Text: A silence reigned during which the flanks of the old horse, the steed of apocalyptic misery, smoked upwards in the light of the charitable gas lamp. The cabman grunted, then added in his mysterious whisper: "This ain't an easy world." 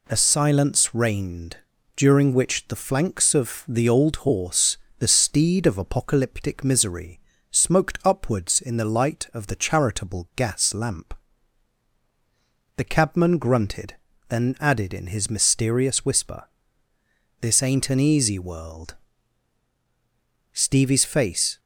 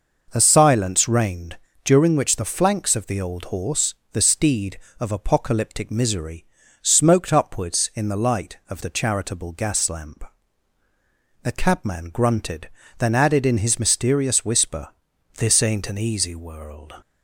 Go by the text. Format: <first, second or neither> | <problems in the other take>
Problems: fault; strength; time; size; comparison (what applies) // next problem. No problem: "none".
second | pauses between "reigned" and "during"; at 1.5 s; 0.38 s long; slight in the second // goes on to say "Stevie's face"; noticeable; from 20.5 s on; 1.0 s long